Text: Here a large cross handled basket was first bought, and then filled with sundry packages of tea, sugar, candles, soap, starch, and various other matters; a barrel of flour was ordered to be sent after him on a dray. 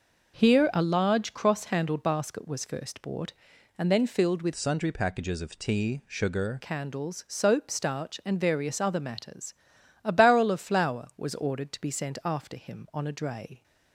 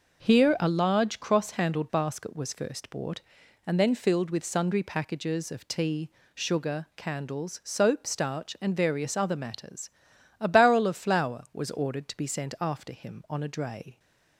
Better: second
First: changes voice from "sundry" to "sugar"; from 4.5 to 6.6 s; 2.1 s long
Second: none

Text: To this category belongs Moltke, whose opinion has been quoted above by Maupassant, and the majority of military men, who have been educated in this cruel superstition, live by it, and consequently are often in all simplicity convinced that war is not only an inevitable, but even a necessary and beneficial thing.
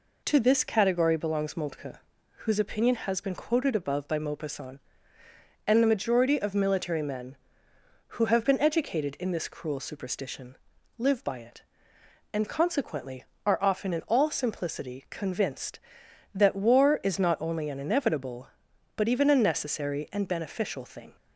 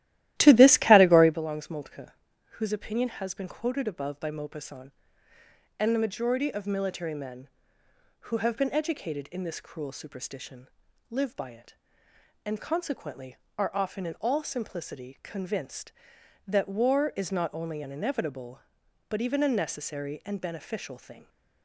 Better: first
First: none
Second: starts louder than the rest; strong; until 1.4 s; 14.5 dB

